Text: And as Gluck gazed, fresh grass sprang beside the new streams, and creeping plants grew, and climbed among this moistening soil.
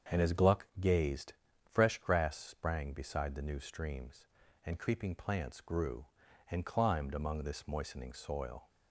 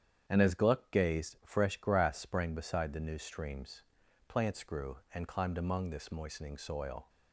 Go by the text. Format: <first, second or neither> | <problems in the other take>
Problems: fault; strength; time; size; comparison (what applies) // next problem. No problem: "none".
first | starts louder than the rest; strong; until 1.2 s; 8.5 dB; strong in the first // skips "and creeping"; at 4.0 s